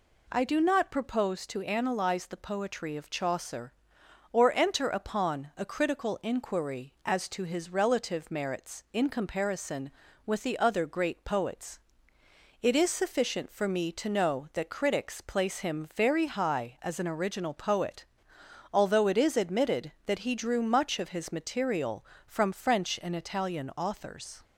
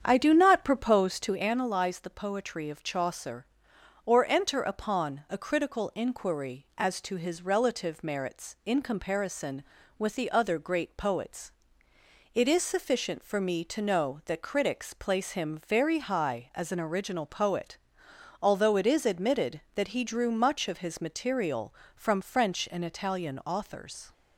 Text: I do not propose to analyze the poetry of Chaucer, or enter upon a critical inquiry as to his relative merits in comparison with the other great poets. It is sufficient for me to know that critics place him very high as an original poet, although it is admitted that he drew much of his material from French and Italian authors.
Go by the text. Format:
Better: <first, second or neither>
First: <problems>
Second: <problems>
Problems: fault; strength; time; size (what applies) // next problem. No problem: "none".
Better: first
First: none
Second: starts louder than the rest; strong; until 1.6 s; 8 dB